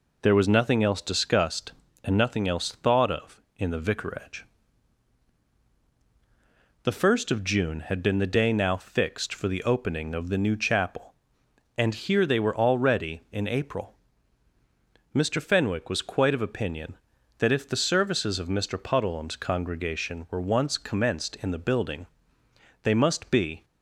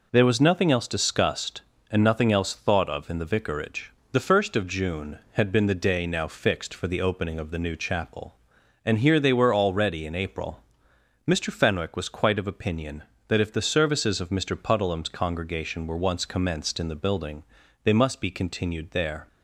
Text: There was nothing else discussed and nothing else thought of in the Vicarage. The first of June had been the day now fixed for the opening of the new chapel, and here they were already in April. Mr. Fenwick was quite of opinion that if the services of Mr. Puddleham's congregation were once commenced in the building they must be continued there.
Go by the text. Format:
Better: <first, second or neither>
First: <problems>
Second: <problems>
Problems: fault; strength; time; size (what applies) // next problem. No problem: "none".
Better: second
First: pauses between "building" and "they"; noticeable; at 22.0 s; 0.76 s long // stops before "continued there"; at 23.6 s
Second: pauses between "building" and "they"; at 17.4 s; 0.40 s long